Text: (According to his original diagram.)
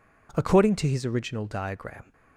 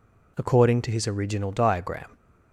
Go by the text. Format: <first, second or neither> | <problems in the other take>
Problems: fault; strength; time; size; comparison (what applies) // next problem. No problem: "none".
neither | none